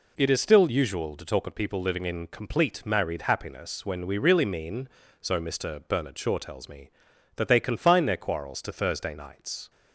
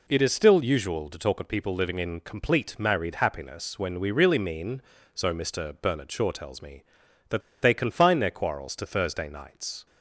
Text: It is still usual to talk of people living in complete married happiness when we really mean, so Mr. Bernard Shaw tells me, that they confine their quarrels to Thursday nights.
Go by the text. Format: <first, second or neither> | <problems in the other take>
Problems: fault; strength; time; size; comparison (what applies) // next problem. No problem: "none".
first | pauses between "that" and "they"; slight; at 7.4 s; 0.21 s long